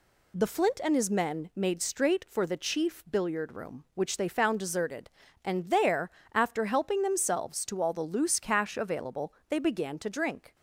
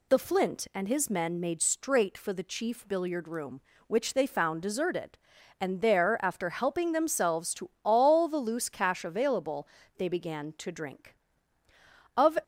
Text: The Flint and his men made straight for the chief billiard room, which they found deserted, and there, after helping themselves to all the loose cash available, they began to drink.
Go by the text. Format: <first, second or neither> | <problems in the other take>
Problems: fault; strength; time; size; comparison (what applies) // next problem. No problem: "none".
first | goes on to say "Of"; slight; from 12.1 s on; 0.22 s long